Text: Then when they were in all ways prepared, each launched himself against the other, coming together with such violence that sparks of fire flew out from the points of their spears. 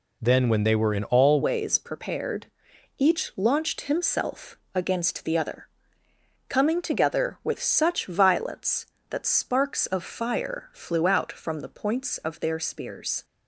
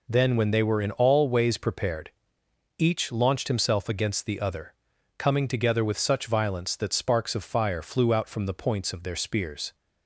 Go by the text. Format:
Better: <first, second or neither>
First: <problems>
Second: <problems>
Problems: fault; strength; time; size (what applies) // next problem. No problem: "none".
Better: second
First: changes voice at "ways"; from 1.4 s on; 11.8 s long // pauses between "himself" and "against"; slight; at 4.5 s; 0.16 s long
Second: none